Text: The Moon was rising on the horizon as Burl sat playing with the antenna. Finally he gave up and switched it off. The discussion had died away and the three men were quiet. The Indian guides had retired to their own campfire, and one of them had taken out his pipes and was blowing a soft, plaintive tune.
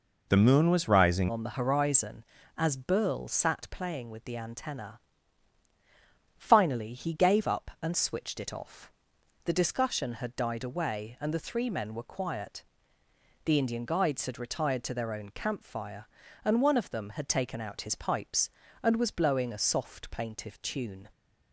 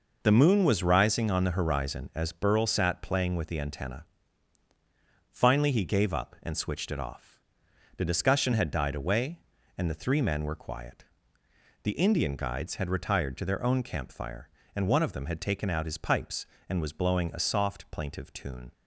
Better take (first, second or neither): second